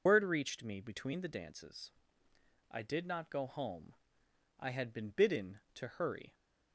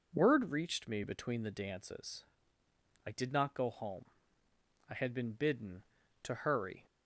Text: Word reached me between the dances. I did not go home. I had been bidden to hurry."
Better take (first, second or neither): second